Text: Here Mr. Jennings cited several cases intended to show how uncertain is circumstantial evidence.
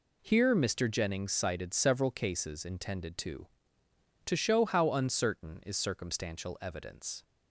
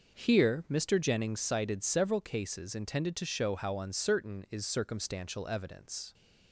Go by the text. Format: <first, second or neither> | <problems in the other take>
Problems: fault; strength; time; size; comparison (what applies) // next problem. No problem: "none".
second | says "to" twice; at 4.2 s